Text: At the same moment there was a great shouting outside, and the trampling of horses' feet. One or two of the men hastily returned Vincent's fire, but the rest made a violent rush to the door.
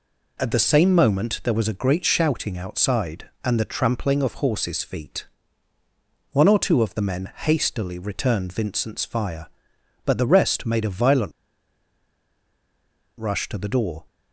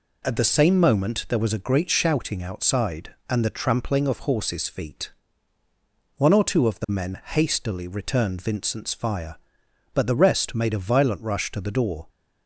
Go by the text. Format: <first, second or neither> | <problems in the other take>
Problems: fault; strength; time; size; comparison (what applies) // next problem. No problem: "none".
second | pauses between "violent" and "rush"; strong; at 11.3 s; 1.8 s long